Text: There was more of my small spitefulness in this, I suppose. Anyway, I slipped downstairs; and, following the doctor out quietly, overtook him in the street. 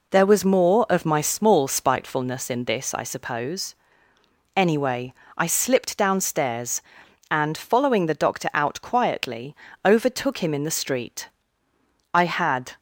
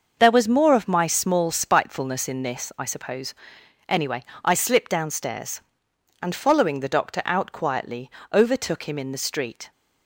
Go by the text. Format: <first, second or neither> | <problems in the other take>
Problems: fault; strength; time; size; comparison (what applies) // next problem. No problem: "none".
second | goes on to say "I had"; noticeable; from 12.1 s on; 0.64 s long